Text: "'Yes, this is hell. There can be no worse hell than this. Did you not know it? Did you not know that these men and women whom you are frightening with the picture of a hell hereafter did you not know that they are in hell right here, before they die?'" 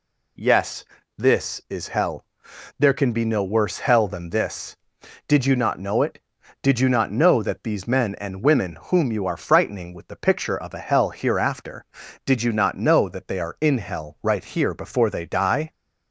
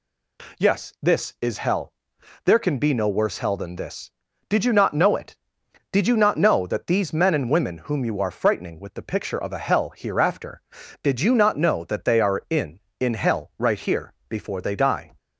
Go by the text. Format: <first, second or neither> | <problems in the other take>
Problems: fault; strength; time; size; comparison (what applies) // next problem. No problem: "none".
first | says "in" twice; at 12.9 s